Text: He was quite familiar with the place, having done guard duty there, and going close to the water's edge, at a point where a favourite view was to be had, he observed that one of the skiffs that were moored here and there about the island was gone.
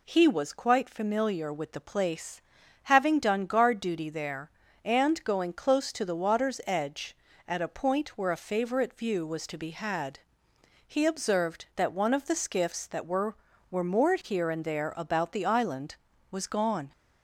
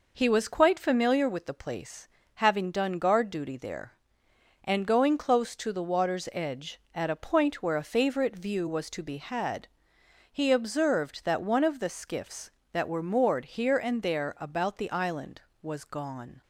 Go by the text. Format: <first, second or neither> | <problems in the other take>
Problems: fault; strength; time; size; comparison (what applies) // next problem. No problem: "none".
second | says "were" twice; at 13.6 s